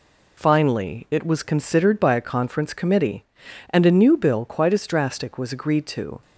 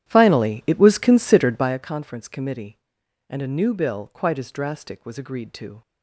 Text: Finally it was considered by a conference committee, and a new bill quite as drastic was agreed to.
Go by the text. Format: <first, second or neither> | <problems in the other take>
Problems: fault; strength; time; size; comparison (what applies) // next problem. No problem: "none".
first | starts louder than the rest; strong; until 1.8 s; 11 dB